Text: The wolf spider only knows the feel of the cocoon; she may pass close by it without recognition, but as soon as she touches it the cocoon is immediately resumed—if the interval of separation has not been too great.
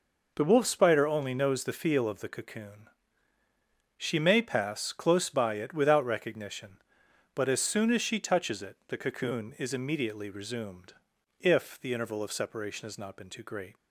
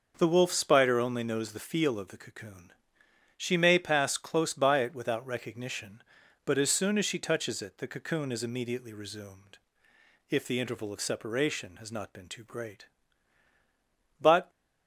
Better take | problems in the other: first | goes on to say "But"; slight; from 14.2 s on; 0.28 s long

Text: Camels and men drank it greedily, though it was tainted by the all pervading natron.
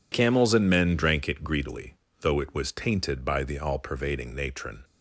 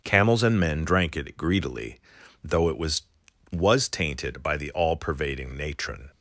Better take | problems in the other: first | starts louder than the rest; until 1.0 s; 6.5 dB // says "was" twice; at 3.5 s

